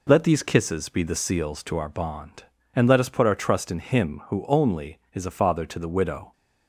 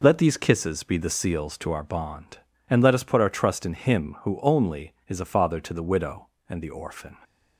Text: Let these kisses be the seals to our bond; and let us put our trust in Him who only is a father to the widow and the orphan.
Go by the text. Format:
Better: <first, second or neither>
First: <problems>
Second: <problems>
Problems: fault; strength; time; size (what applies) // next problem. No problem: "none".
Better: second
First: stops before "and the orphan"; at 6.3 s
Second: none